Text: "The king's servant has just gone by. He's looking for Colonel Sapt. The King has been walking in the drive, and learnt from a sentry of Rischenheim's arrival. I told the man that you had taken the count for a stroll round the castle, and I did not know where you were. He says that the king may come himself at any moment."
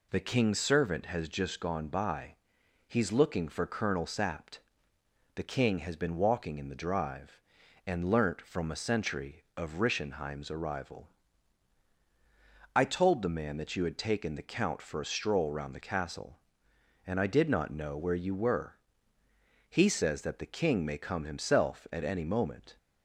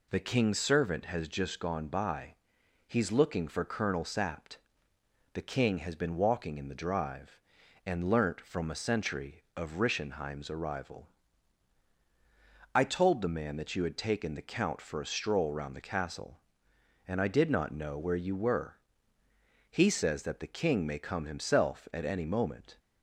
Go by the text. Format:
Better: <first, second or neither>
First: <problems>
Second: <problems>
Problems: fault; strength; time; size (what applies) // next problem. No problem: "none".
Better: neither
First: none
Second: none